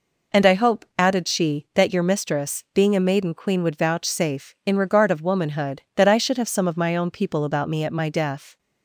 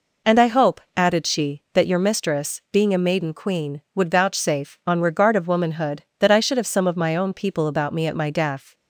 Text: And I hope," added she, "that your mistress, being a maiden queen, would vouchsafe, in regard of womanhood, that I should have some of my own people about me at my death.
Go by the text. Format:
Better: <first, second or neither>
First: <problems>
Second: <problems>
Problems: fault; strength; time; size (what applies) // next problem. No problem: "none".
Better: first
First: none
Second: says "on" for "in"; at 4.8 s